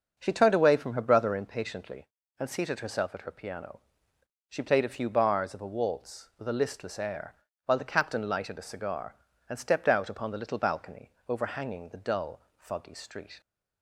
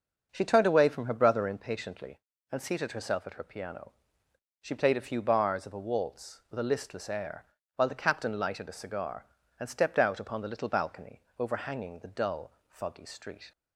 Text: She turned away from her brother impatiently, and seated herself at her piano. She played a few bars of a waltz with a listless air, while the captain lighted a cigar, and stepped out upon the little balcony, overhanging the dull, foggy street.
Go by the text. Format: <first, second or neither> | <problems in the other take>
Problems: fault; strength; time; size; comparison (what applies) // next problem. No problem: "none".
neither | starts louder than the rest; the same in both